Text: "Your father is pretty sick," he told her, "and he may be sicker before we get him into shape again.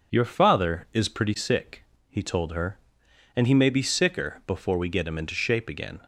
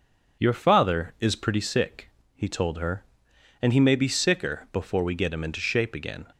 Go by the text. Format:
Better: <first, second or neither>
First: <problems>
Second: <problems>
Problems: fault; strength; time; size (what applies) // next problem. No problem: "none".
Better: neither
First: none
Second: none